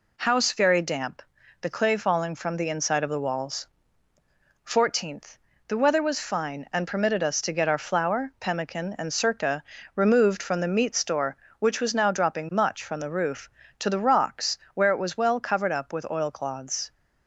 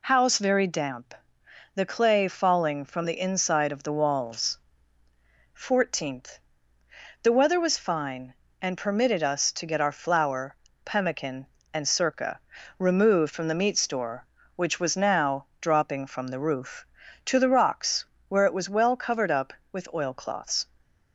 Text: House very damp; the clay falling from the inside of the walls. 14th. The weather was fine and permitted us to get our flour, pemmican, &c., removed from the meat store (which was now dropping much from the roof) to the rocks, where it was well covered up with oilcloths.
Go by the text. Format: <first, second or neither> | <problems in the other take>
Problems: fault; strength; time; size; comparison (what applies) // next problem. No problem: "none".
first | skips "much"; at 16.0 s